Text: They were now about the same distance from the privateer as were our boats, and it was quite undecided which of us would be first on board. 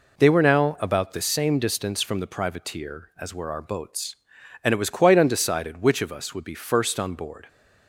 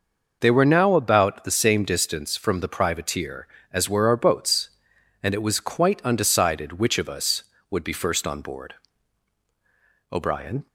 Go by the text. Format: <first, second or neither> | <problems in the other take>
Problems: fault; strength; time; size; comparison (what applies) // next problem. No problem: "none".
first | goes on to say "O'Brien"; from 10.1 s on; 0.54 s long